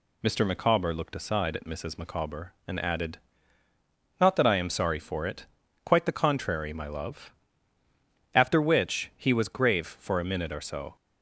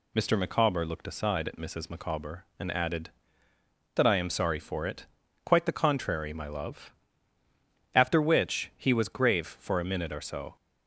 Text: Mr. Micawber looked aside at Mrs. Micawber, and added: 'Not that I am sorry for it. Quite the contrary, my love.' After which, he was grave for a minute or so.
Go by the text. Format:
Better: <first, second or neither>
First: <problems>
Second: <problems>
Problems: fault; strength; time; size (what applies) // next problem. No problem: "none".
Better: first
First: none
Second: skips "Not"; at 3.5 s